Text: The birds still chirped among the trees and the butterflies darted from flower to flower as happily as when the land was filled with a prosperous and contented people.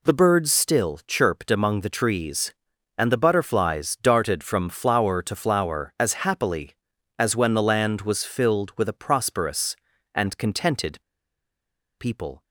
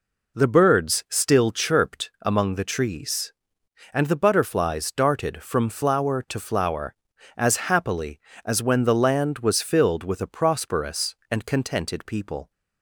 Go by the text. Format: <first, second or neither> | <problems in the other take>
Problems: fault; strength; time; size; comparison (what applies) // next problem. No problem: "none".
second | pauses between "contented" and "people"; at 10.9 s; 1.0 s long